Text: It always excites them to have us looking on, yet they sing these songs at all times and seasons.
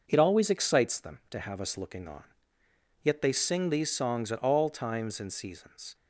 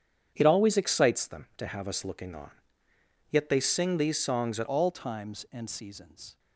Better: first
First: none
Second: starts louder than the rest; strong; until 1.3 s; 8.5 dB // changes voice at "all"; from 4.6 s on; 1.7 s long

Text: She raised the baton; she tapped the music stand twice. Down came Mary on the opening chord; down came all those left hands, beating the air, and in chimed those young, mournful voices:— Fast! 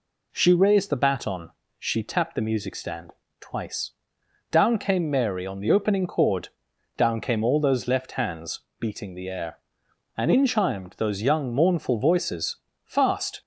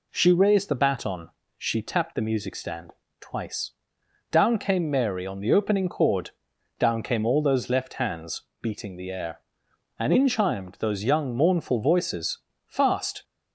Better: neither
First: pauses between "stand" and "twice"; slight; at 3.1 s; 0.30 s long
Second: pauses between "stand" and "twice"; slight; at 2.9 s; 0.30 s long

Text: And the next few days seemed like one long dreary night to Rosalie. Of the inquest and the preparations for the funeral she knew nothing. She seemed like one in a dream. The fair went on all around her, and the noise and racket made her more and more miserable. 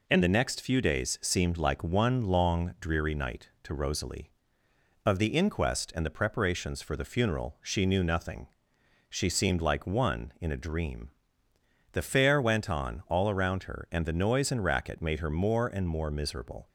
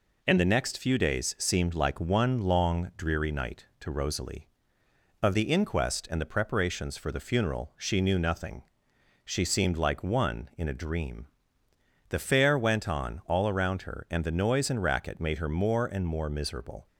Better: neither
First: none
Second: none

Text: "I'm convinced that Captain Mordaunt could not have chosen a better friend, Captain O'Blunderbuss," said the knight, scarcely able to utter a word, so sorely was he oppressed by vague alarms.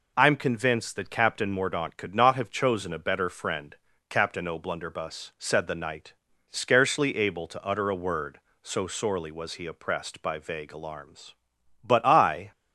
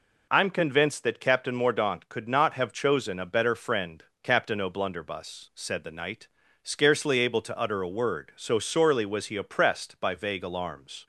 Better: second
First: goes on to say "But I"; noticeable; from 11.8 s on; 0.68 s long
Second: none

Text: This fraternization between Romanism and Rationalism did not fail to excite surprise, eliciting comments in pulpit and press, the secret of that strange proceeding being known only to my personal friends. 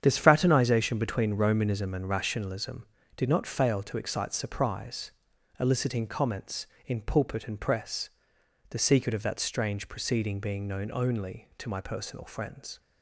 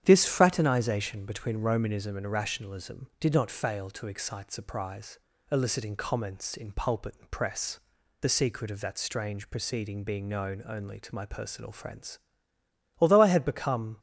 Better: first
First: starts louder than the rest; strong; until 1.0 s; 8.5 dB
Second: starts louder than the rest; strong; until 1.0 s; 9.5 dB // goes on to say "Although I had become"; noticeable; from 12.9 s on; 1.0 s long

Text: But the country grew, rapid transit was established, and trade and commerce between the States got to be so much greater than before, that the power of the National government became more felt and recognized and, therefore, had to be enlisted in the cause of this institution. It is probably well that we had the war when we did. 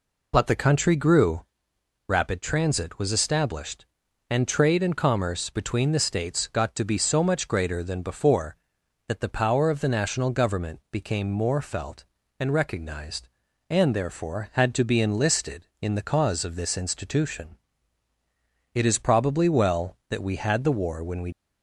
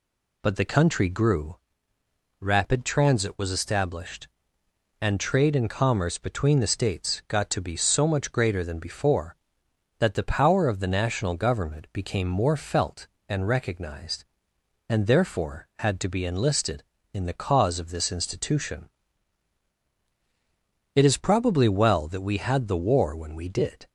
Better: second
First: stops before "did"; at 21.3 s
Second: none

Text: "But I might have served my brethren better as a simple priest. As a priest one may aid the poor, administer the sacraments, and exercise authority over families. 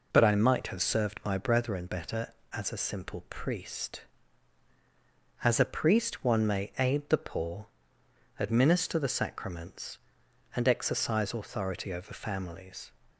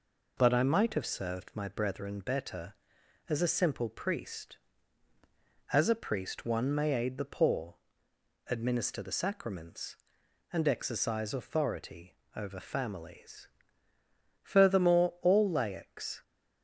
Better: first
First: none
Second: pauses between "authority" and "over"; slight; at 12.1 s; 0.18 s long // goes on to say "Furthermore all laics"; strong; from 14.4 s on; 1.7 s long

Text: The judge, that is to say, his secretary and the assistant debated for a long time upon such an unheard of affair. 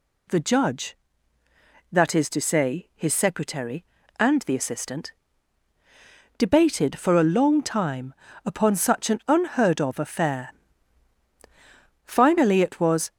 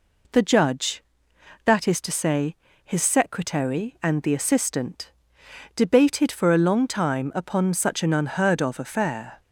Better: second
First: pauses between "assistant" and "debated"; strong; at 5.1 s; 1.2 s long // pauses between "time" and "upon"; slight; at 8.1 s; 0.30 s long // goes on to say "Finally it was"; noticeable; from 12.0 s on; 1.0 s long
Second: pauses between "assistant" and "debated"; noticeable; at 5.1 s; 0.64 s long

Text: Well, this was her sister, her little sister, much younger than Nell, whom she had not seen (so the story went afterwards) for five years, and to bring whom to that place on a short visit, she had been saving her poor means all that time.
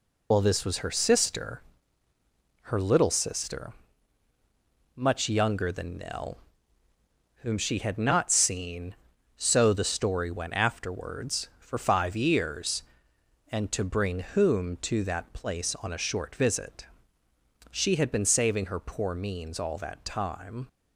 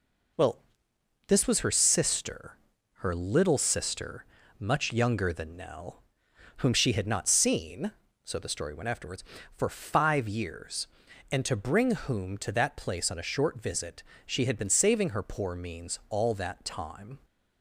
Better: second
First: loses the start of "Well"; at 0.3 s; 25 ms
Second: none

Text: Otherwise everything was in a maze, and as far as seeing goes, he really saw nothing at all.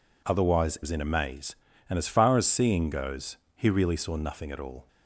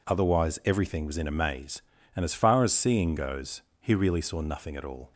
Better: second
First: skips "everything"; at 0.8 s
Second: none

